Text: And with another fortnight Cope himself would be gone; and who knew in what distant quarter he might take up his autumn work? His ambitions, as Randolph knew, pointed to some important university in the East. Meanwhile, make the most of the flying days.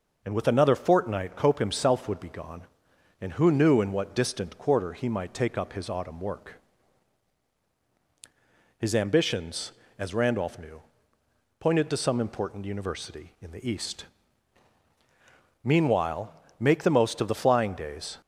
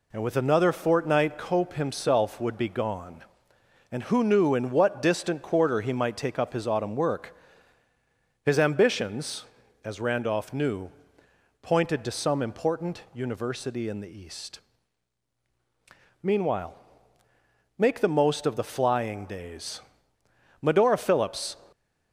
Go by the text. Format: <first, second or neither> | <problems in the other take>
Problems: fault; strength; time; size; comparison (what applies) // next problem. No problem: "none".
first | goes on to say "Medora Phillips"; noticeable; from 20.6 s on; 0.94 s long